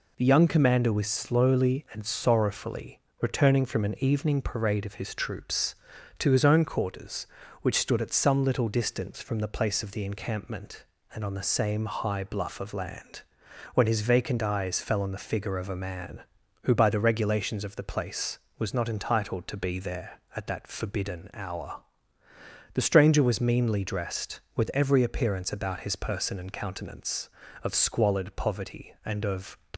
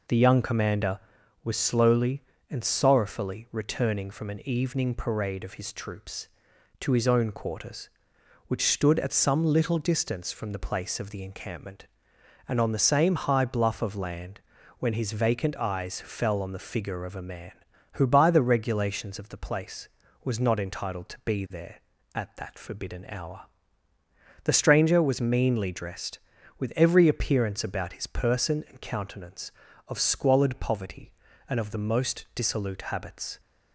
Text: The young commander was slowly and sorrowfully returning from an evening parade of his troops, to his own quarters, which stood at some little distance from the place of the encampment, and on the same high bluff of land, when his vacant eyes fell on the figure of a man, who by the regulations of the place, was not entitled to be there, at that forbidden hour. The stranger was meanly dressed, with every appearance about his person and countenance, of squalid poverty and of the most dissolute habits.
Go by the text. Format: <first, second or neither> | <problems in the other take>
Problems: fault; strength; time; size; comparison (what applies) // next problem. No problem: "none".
second | pauses between "sorrowfully" and "returning"; slight; at 3.0 s; 0.20 s long // stops before "the most dissolute habits"; at 29.7 s